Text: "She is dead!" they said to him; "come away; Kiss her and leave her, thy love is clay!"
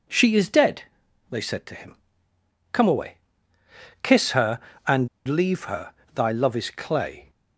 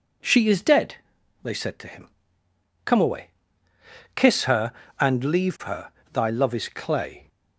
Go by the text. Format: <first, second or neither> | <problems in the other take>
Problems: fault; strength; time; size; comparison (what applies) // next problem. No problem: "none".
second | pauses between "and" and "leave"; slight; at 5.0 s; 0.19 s long